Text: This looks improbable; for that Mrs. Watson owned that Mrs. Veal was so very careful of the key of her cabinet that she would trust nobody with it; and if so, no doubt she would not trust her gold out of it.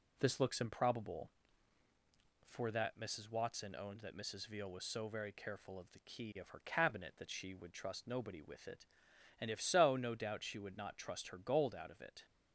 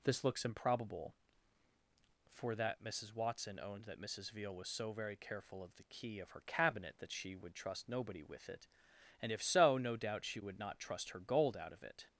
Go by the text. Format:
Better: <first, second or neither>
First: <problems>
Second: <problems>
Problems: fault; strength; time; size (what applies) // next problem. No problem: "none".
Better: second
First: gets quieter; slight; throughout; 2.5 dB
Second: none